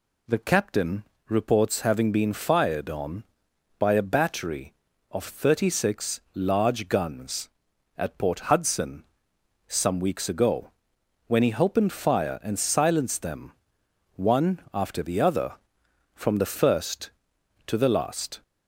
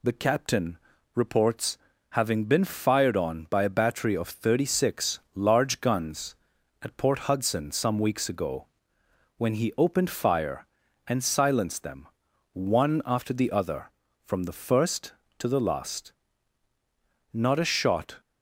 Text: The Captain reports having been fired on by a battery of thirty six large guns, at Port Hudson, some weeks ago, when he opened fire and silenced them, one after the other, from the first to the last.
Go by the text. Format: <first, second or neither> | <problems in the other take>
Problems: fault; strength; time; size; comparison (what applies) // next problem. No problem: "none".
first | pauses between "Captain" and "reports"; slight; at 0.7 s; 0.36 s long; slight in the first // pauses between "reports" and "having"; slight; at 1.7 s; 0.34 s long // pauses between "six" and "large"; slight; at 5.1 s; 0.16 s long // goes on to say "Not a shot"; noticeable; from 17.3 s on; 0.86 s long